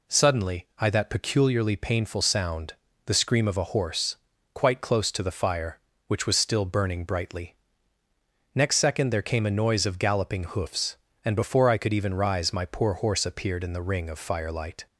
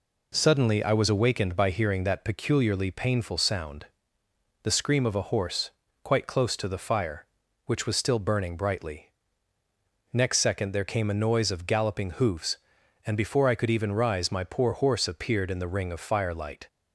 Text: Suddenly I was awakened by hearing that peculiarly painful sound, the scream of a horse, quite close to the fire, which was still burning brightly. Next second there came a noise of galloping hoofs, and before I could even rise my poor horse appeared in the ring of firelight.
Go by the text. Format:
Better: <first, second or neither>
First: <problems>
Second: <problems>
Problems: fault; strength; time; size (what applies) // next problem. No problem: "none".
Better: second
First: skips "was awakened by hearing"; at 0.8 s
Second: none